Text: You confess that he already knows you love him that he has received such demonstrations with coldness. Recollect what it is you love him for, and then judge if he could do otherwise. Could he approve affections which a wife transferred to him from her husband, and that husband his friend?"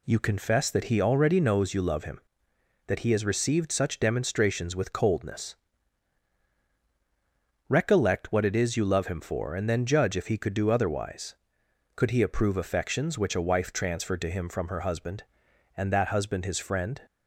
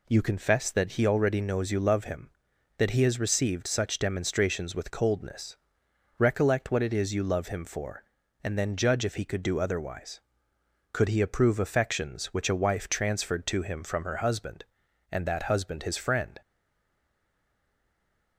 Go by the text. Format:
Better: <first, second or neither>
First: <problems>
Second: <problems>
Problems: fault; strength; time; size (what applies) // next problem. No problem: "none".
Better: first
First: none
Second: stays silent after the last word; noticeable; from 16.4 s on; 1.9 s long